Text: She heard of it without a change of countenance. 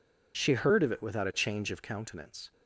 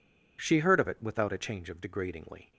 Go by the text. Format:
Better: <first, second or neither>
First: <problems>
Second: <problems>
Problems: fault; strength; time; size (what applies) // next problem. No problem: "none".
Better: first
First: none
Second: says "degradingly" for "countenance"; at 1.7 s